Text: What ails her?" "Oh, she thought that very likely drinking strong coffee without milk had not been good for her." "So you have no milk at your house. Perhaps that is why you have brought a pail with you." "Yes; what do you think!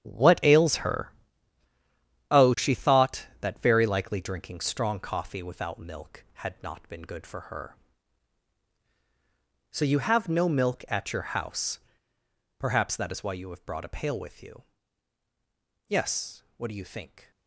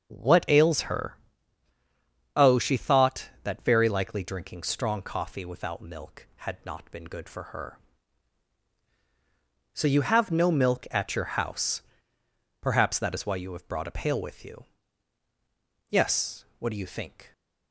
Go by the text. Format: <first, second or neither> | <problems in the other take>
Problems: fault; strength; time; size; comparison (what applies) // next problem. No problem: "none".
second | gets quieter; strong; throughout; 11 dB // starts louder than the rest; strong; until 2.4 s; 10.5 dB; strong in the second